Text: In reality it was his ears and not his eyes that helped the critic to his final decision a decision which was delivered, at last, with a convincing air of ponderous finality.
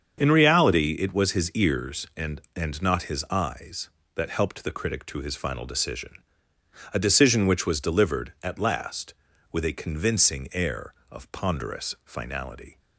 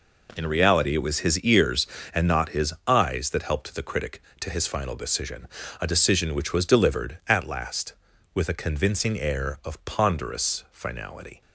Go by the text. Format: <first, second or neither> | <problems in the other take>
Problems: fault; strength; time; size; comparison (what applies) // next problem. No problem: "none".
second | starts louder than the rest; until 1.2 s; 7 dB // says "and" twice; at 2.5 s // pauses between "decision" and "a"; noticeable; at 6.1 s; 0.82 s long; slight in the second